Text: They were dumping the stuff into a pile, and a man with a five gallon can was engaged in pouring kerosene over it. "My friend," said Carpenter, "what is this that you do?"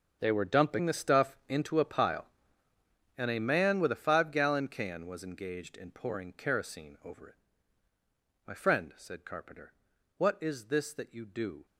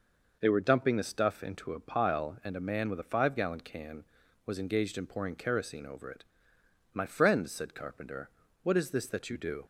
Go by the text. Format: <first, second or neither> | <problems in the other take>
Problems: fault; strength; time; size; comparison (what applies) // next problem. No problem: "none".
second | gets quieter; strong; throughout; 16 dB